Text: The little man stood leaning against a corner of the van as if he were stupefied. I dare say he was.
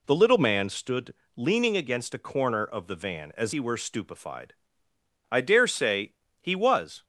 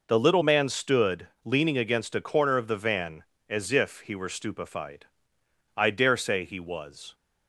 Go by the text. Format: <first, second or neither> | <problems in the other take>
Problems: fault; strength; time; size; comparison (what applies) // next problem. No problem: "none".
second | pauses between "stood" and "leaning"; slight; at 1.1 s; 0.22 s long; slight in the second // skips "if"; at 3.5 s // pauses between "say" and "he"; slight; at 6.1 s; 0.28 s long